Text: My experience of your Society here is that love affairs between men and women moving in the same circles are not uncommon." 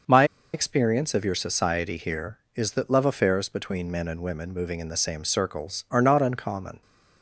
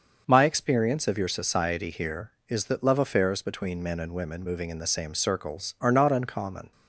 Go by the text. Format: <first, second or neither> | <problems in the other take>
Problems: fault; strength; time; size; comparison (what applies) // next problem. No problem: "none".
second | starts louder than the rest; until 1.3 s; 6 dB; also in the second // pauses between "My" and "experience"; slight; at 0.2 s; 0.29 s long